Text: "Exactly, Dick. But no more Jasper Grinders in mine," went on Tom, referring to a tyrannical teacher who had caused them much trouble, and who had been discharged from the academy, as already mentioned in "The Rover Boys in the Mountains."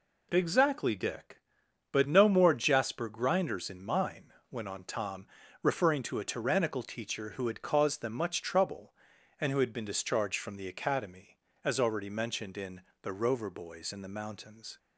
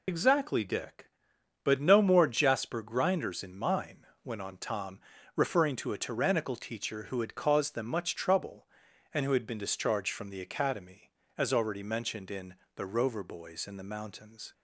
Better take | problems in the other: first | loses the start of "Exactly"; at 0.0 s; 85 ms // pauses between "in" and "The"; slight; at 12.5 s; 0.22 s long; slight in the first

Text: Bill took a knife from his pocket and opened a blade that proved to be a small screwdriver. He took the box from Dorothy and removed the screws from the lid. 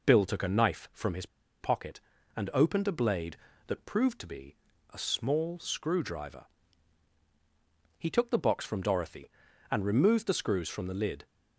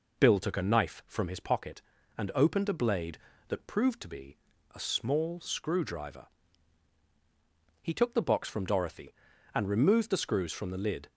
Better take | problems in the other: second | pauses between "his" and "pocket"; slight; at 1.2 s; 0.35 s long // pauses between "be" and "a"; slight; at 4.5 s; 0.36 s long; slight in the second

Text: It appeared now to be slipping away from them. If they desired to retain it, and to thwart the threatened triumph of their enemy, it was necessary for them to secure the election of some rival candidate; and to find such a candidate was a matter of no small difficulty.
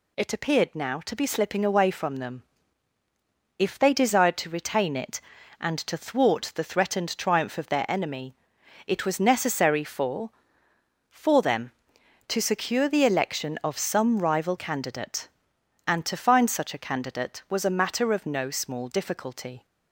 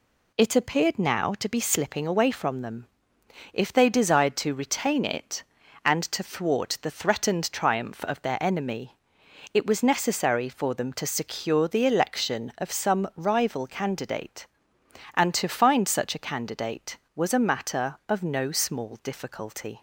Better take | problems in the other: second | says "for" twice; at 11.1 s

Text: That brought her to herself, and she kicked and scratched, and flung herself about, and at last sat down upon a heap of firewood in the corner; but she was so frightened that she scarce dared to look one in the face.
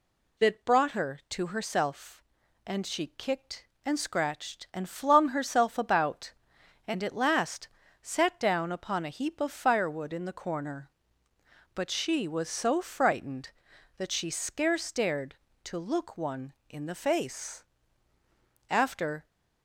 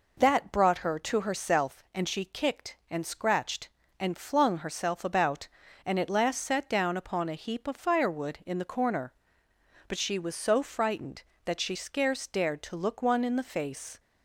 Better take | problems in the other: second | pauses between "last" and "sat"; slight; at 7.6 s; 0.34 s long // goes on to say "After"; from 18.7 s on; 0.54 s long

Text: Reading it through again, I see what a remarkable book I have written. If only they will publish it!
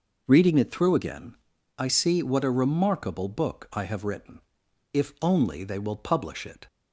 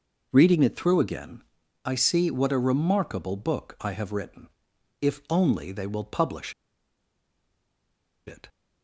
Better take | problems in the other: first | pauses between "publish" and "it"; strong; at 6.5 s; 1.7 s long

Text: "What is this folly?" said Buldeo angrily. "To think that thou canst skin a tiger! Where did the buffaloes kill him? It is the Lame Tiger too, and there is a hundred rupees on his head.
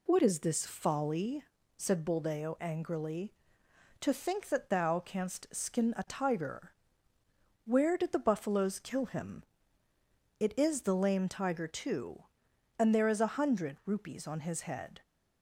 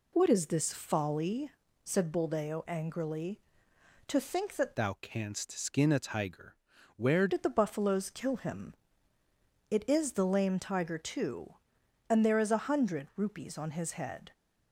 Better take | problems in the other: first | changes voice from "thou" to "Where"; from 4.7 to 7.2 s; 2.5 s long

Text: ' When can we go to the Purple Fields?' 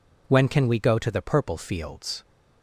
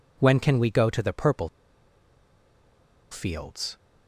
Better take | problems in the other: first | pauses between "Purple" and "Fields"; strong; at 1.4 s; 1.6 s long

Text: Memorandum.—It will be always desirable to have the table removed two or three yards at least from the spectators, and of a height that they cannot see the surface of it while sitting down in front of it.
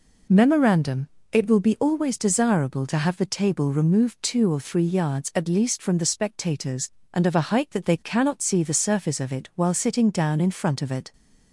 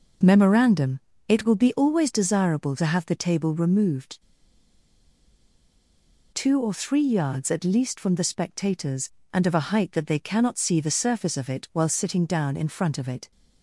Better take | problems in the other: first | pauses between "removed" and "two"; strong; at 4.1 s; 2.1 s long

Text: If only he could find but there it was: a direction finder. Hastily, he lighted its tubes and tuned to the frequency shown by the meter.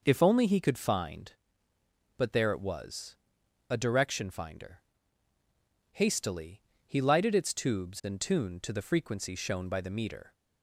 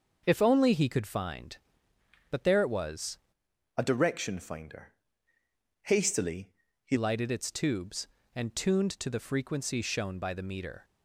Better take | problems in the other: first | starts louder than the rest; until 1.2 s; 6 dB // changes voice from "a" to "he"; from 3.7 to 6.9 s; 3.2 s long

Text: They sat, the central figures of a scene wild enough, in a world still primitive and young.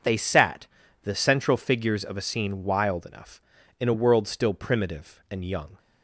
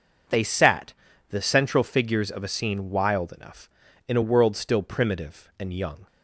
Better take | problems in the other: neither | none

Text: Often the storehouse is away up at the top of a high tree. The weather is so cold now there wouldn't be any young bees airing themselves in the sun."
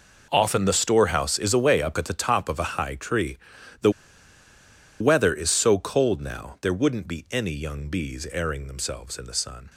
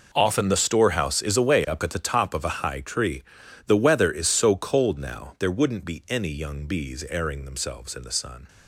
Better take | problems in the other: second | pauses between "The" and "weather"; at 3.9 s; 1.0 s long

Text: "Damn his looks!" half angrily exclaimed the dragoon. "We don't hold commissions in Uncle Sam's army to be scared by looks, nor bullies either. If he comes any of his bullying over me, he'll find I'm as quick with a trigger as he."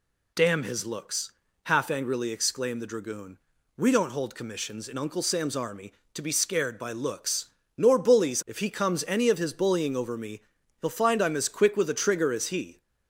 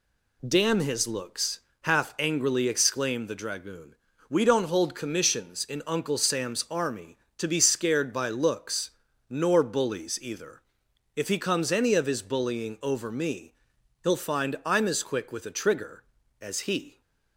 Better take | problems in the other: second | skips "either"; at 8.4 s

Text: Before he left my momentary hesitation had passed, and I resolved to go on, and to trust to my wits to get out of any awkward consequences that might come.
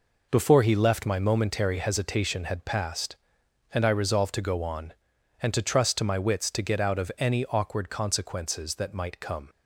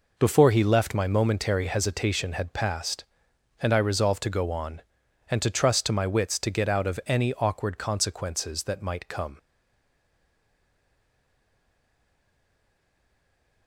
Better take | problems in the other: first | stays silent after the last word; strong; from 9.3 s on; 4.3 s long

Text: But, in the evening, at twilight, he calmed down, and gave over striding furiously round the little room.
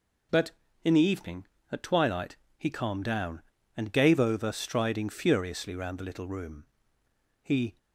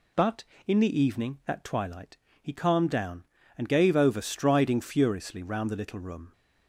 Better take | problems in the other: second | goes on to say "He"; slight; from 7.4 s on; 0.34 s long

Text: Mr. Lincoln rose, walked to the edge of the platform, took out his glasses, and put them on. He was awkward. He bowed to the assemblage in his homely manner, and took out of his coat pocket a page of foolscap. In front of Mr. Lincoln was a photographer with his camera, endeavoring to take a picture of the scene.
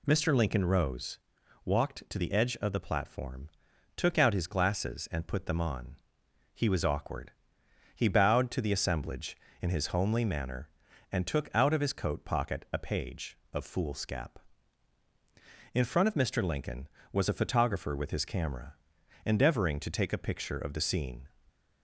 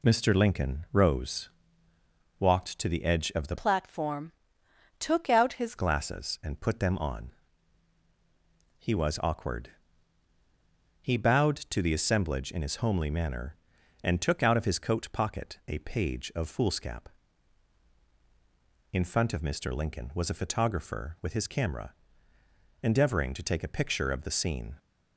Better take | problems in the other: first | changes voice from "platform" to "his"; from 3.5 to 5.7 s; 2.2 s long

